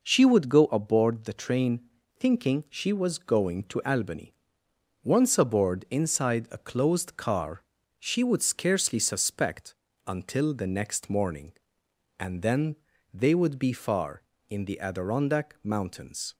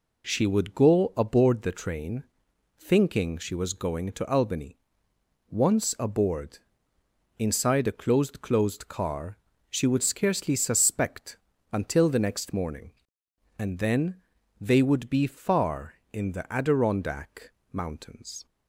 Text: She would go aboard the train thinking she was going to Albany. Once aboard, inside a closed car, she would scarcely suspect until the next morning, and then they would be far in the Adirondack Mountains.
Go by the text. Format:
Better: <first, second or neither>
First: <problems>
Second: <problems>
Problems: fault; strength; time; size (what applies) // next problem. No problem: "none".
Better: first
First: pauses between "train" and "thinking"; at 1.8 s; 0.38 s long // pauses between "suspect" and "until"; slight; at 9.7 s; 0.32 s long // pauses between "then" and "they"; slight; at 12.7 s; 0.36 s long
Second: pauses between "train" and "thinking"; noticeable; at 2.2 s; 0.56 s long // says "closed" twice; at 8.4 s // pauses between "suspect" and "until"; slight; at 11.3 s; 0.34 s long // pauses between "then" and "they"; at 14.1 s; 0.44 s long // pauses between "Adirondack" and "Mountains"; slight; at 17.5 s; 0.20 s long